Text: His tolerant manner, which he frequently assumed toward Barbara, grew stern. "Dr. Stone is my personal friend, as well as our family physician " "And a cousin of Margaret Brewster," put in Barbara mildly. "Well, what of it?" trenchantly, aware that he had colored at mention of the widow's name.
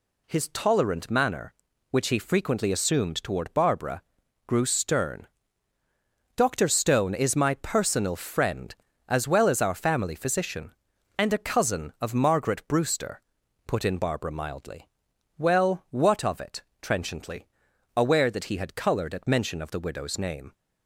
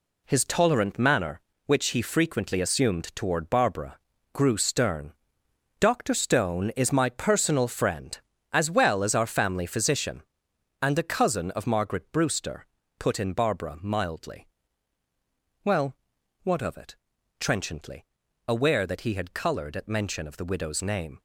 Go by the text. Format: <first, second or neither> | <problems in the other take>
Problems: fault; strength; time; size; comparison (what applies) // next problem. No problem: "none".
first | gets quieter; strong; throughout; 7.5 dB